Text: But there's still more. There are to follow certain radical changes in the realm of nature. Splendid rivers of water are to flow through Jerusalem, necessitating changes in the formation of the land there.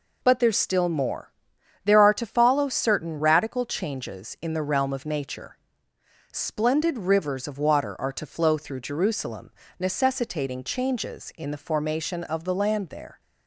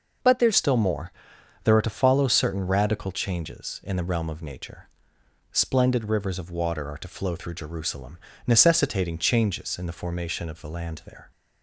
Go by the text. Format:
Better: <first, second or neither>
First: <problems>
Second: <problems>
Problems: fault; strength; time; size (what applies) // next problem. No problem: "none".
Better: first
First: none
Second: changes voice at "still"; from 0.5 s on; 10.8 s long